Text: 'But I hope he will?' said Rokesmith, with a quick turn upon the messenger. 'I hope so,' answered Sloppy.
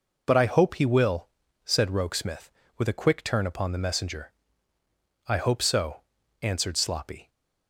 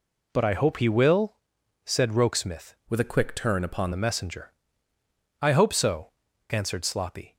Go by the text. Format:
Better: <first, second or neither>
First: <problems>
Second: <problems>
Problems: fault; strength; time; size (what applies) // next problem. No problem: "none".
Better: first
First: none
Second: changes voice from "with" to "upon"; from 2.8 to 3.9 s; 1.1 s long